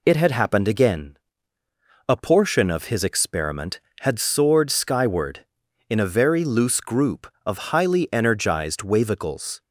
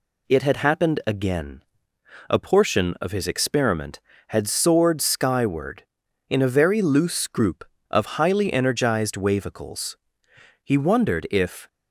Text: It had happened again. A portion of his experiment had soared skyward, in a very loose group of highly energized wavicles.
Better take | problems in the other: first | goes on to say "He wondered if"; noticeable; from 10.6 s on; 1.0 s long

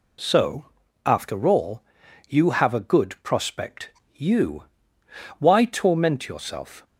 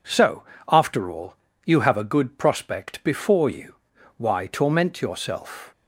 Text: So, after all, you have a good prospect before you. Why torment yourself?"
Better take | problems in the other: second | skips "before"; at 4.0 s

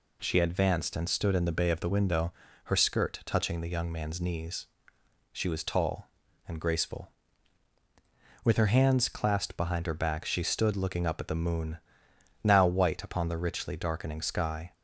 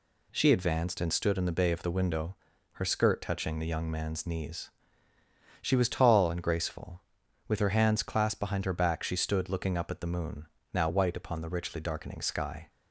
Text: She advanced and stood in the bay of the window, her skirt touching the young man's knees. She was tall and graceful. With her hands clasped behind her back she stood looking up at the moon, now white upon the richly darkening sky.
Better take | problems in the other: neither | none

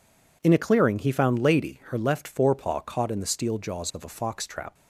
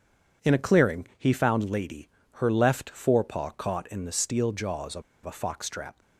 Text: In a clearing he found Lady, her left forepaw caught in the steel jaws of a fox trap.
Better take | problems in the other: first | pauses between "of" and "a"; slight; at 5.0 s; 0.21 s long

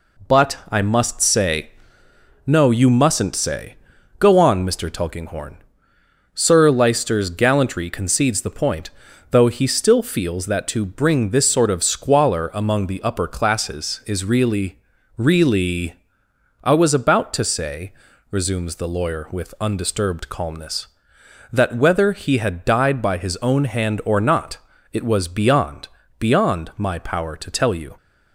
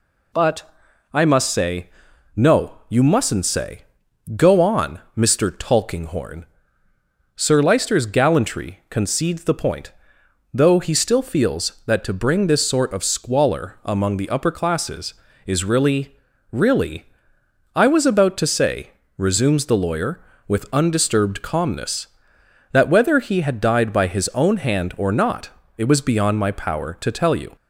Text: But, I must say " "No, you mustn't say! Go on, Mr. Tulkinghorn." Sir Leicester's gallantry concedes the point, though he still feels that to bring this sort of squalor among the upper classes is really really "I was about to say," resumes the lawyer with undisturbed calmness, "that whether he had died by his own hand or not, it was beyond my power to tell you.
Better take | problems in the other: second | pauses between "really" and "really"; at 14.7 s; 0.38 s long; slight in the second // pauses between "really" and "I"; noticeable; at 15.9 s; 0.66 s long; noticeable in the second // says "beyond" twice; at 26.1 s

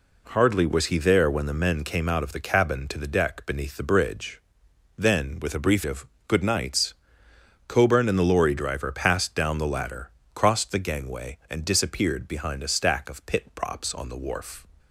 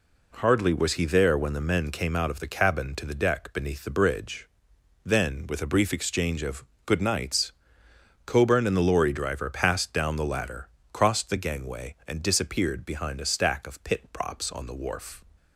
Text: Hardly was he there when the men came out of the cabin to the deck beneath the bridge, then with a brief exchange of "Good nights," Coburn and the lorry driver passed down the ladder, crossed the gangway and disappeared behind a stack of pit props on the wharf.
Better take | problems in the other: second | skips "exchange"; at 5.8 s // pauses between "of" and "Good"; slight; at 6.0 s; 0.20 s long; slight in the second

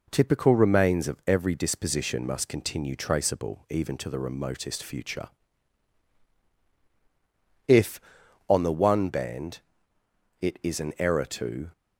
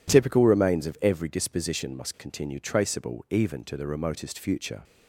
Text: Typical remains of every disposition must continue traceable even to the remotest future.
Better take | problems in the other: second | goes on to say "If on the one band it is an error to"; strong; from 7.6 s on; 4.0 s long

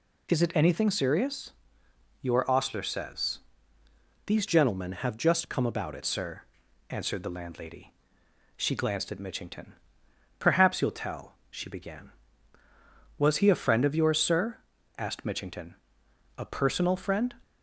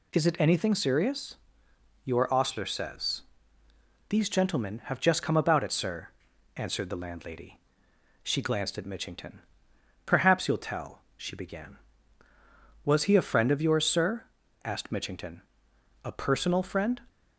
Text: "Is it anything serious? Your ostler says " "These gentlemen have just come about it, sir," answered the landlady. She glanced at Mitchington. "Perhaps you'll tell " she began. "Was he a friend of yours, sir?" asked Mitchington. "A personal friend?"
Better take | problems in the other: second | changes voice from "gentlemen" to "it"; from 4.4 to 6.0 s; 1.6 s long

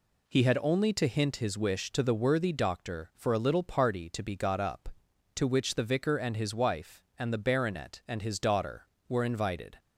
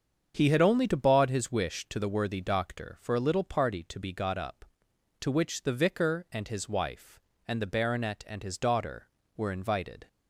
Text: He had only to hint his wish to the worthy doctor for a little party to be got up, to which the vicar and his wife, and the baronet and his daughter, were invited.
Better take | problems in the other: first | starts louder than the rest; strong; until 1.3 s; 7.5 dB // says "baud" for "hint"; at 0.9 s

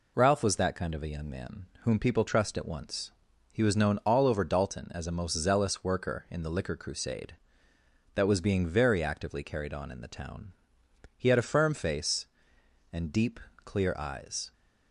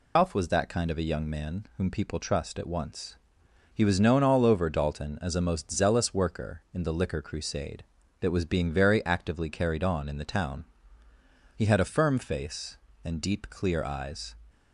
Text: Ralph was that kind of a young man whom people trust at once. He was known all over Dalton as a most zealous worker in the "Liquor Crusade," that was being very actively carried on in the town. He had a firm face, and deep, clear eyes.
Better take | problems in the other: first | loses the start of "Ralph"; at 0.1 s; 130 ms

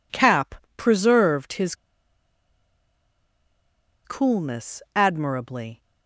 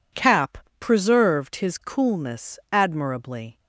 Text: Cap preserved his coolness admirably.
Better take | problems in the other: second | pauses between "Cap" and "preserved"; slight; at 0.5 s; 0.20 s long; slight in the second // pauses between "his" and "coolness"; strong; at 1.7 s; 2.3 s long

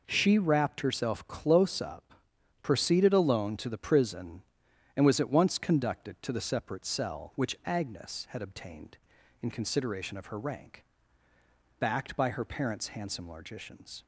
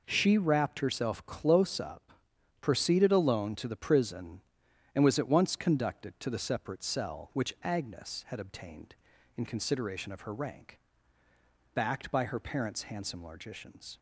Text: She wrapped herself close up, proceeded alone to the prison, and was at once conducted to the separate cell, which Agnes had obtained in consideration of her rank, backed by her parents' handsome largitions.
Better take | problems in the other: neither | none

